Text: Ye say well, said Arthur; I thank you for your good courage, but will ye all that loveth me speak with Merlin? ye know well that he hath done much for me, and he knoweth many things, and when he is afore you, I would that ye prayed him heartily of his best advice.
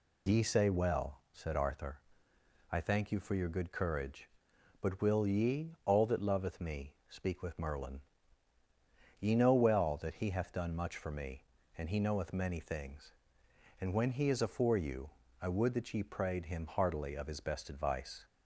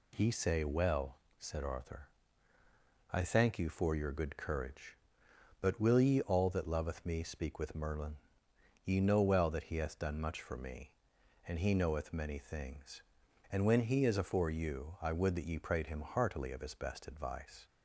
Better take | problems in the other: neither | none

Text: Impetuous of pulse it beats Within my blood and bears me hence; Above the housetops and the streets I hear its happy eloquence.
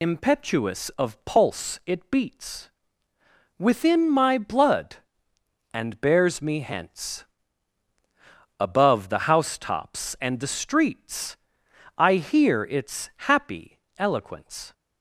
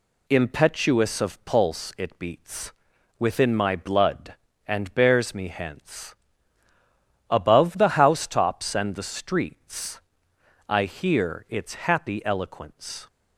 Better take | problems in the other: second | loses the start of "Impetuous"; at 0.0 s; 45 ms // pauses between "beats" and "Within"; noticeable; at 2.6 s; 0.90 s long; also in the second // pauses between "streets" and "I"; noticeable; at 11.3 s; 0.60 s long; noticeable in the second // pauses between "its" and "happy"; slight; at 13.0 s; 0.20 s long // pauses between "happy" and "eloquence"; slight; at 13.7 s; 0.18 s long

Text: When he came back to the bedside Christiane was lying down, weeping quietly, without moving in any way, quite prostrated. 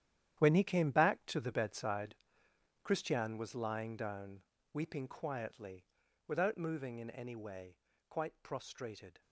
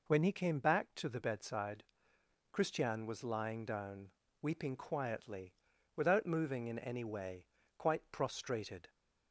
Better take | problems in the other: second | gets quieter; strong; throughout; 13 dB // pauses between "bedside" and "Christiane"; noticeable; at 2.1 s; 0.66 s long; noticeable in the second

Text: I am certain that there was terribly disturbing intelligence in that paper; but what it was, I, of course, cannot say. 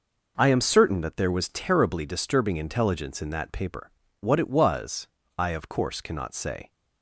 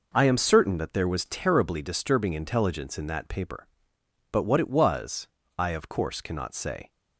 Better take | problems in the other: second | skips "but"; at 4.0 s

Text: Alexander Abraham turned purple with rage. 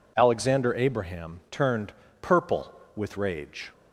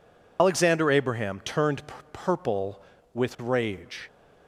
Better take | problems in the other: first | loses the start of "Alexander"; at 0.3 s; 85 ms // pauses between "turned" and "purple"; slight; at 1.8 s; 0.28 s long; slight in the first

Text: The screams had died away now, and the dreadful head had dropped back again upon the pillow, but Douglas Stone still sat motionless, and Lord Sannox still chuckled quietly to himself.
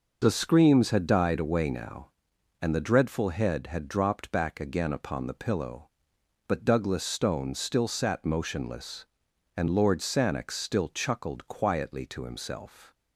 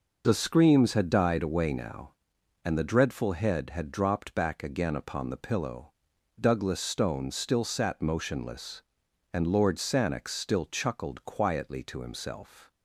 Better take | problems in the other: first | skips "but"; at 6.1 s

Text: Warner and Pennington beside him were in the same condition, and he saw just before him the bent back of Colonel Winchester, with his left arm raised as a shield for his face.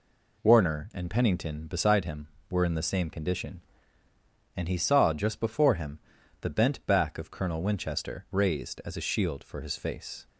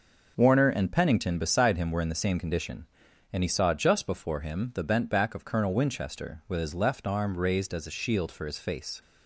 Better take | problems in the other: second | pauses between "him" and "the"; at 5.9 s; 0.42 s long // skips "with his left arm"; at 8.2 s

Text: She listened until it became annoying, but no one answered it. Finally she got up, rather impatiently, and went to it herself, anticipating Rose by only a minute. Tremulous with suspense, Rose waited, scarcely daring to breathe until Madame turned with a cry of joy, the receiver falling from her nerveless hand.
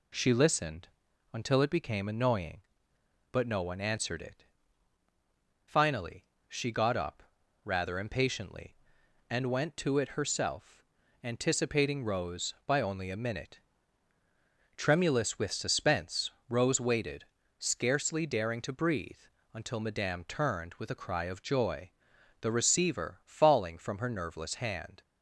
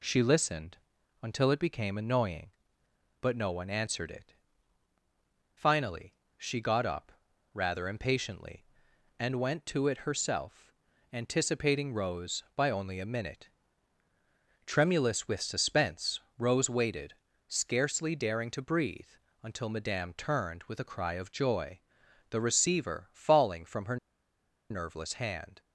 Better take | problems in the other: first | pauses between "listened" and "until"; at 0.7 s; 0.44 s long; also in the first // pauses between "Finally" and "she"; slight; at 6.1 s; 0.24 s long; slight in the first // pauses between "breathe" and "until"; slight; at 19.1 s; 0.28 s long; slight in the first // pauses between "her" and "nerveless"; noticeable; at 23.9 s; 0.73 s long

